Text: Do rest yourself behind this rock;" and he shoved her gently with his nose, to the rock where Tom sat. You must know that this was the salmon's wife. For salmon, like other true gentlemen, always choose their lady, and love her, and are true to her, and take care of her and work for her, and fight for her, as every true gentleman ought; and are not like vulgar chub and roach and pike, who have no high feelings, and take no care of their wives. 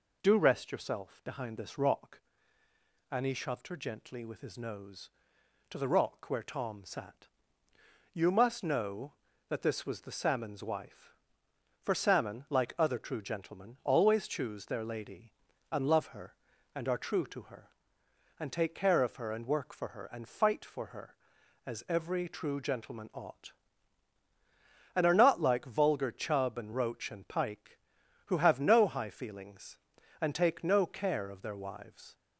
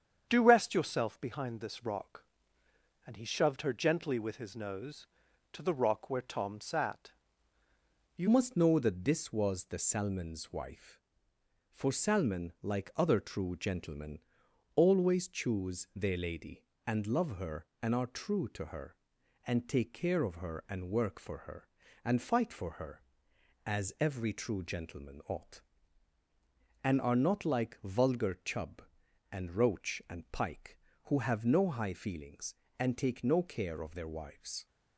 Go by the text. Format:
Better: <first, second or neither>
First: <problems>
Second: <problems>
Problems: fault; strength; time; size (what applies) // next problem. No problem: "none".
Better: first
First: none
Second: starts louder than the rest; strong; until 1.3 s; 8 dB // changes voice at "must"; from 8.2 s on; 26.4 s long